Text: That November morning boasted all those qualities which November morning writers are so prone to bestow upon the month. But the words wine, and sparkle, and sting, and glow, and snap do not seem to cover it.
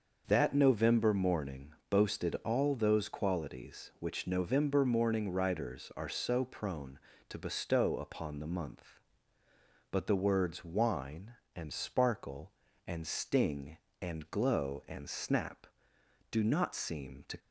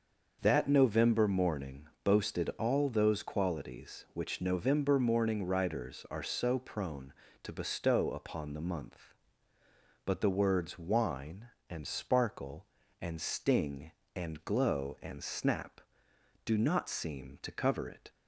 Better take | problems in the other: second | starts louder than the rest; until 1.2 s; 6 dB; also in the second // pauses between "morning" and "boasted"; slight; at 1.7 s; 0.18 s long; slight in the second // stops before "cover it"; at 17.3 s

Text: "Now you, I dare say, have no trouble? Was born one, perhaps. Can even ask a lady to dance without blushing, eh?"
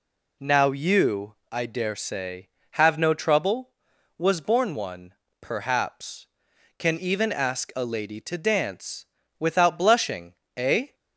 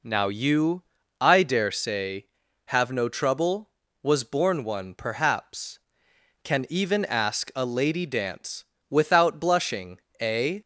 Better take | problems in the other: first | skips "to"; at 8.0 s // pauses between "dance" and "without"; slight; at 8.6 s; 0.26 s long; slight in the first

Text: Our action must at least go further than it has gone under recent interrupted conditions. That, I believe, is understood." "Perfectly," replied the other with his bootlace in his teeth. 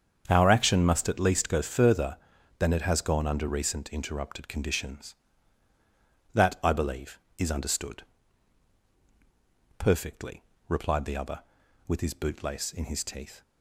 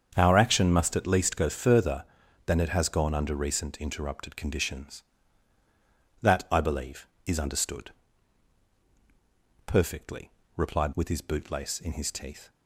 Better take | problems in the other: first | starts louder than the rest; strong; until 1.1 s; 7.5 dB; strong in the first // skips "the other"; at 10.9 s

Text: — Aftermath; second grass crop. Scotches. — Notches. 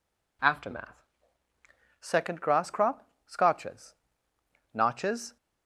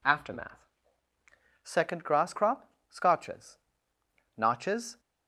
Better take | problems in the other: neither | none

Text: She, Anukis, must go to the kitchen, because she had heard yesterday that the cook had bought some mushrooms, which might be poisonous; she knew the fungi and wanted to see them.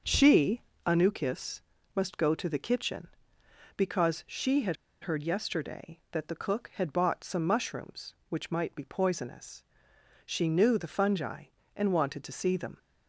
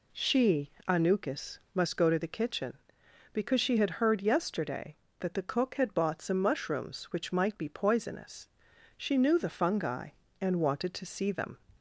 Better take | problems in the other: second | starts louder than the rest; noticeable; until 1.3 s; 6 dB // pauses between "had" and "heard"; slight; at 4.7 s; 0.26 s long

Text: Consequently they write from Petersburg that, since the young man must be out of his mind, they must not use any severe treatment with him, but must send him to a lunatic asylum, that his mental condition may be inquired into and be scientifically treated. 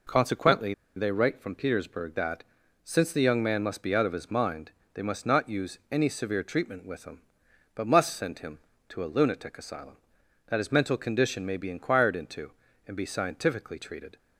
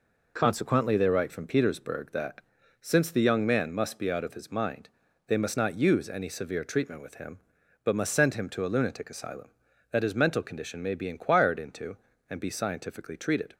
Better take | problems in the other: second | pauses between "Consequently" and "they"; slight; at 0.7 s; 0.22 s long

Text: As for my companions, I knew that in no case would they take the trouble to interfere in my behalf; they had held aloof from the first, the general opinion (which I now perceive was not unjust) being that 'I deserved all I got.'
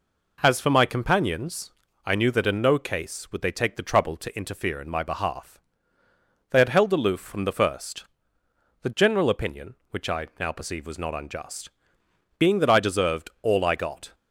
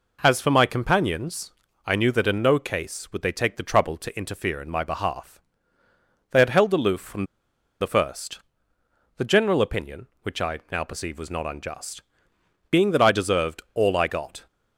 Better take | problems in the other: first | pauses between "from" and "the"; noticeable; at 7.2 s; 0.57 s long

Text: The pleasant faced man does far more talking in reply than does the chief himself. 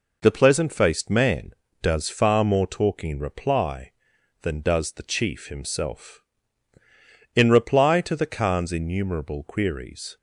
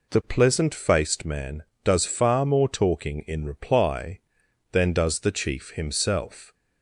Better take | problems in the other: second | goes on to say "In reply to the khan's innumerable queries"; strong; from 7.3 s on; 2.8 s long

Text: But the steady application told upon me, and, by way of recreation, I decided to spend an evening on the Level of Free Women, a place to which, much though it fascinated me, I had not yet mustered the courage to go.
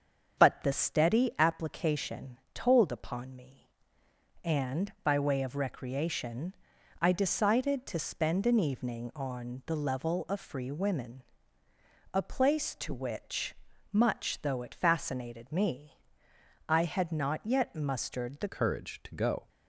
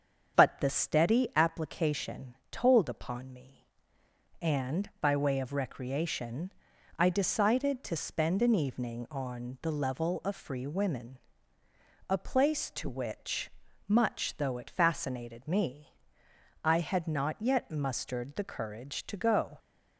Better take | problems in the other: second | starts louder than the rest; strong; until 1.4 s; 7.5 dB; strong in the second // pauses between "application" and "told"; slight; at 2.3 s; 0.18 s long; slight in the second // changes voice at "courage"; from 18.4 s on; 1.0 s long

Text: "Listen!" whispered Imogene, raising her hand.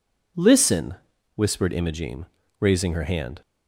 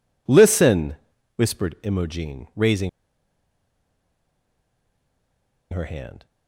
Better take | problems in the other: first | pauses between "raising" and "her"; strong; at 2.8 s; 2.8 s long

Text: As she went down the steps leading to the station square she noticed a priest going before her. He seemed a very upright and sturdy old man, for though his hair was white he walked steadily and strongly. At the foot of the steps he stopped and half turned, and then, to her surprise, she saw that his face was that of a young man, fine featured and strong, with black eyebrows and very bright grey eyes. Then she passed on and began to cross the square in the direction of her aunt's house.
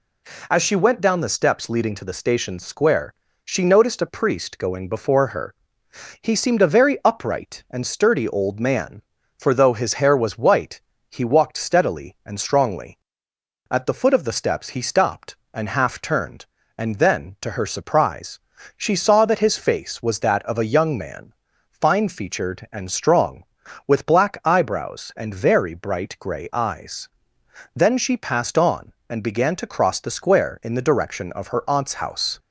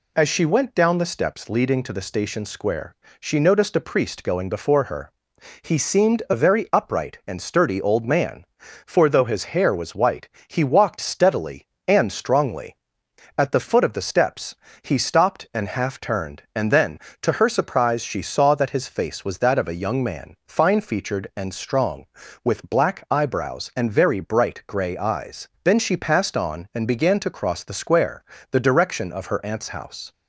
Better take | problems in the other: first | pauses between "square" and "she"; slight; at 2.9 s; 0.24 s long; slight in the first // pauses between "white" and "he"; slight; at 10.2 s; 0.18 s long; slight in the first // pauses between "steps" and "he"; slight; at 14.5 s; 0.30 s long // skips "in"; at 28.3 s

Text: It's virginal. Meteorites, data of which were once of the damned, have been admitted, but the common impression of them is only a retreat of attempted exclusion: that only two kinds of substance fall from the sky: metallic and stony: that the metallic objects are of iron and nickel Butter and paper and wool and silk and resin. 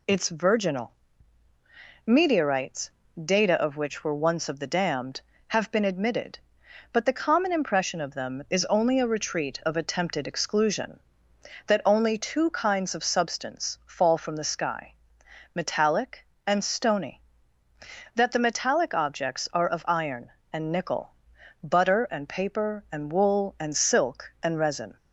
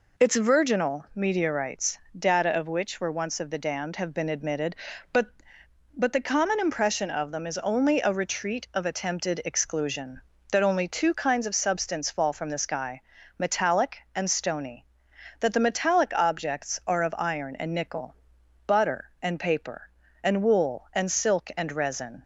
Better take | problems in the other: first | says "but" twice; at 5.9 s // pauses between "nickel" and "Butter"; noticeable; at 18.1 s; 0.52 s long; noticeable in the first

